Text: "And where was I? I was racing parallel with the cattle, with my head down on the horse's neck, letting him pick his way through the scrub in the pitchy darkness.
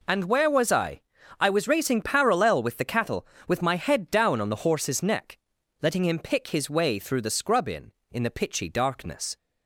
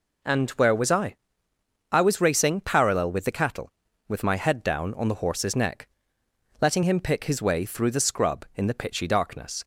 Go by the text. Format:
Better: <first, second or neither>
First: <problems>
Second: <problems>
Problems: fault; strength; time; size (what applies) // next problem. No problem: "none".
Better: second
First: says "in" twice; at 8.1 s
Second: none